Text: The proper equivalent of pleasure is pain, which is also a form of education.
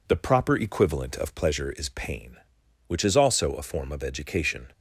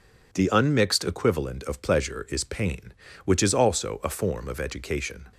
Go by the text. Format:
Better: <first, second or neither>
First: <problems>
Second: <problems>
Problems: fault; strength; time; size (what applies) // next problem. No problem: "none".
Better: first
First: none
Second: says "unmixed" for "proper"; at 0.4 s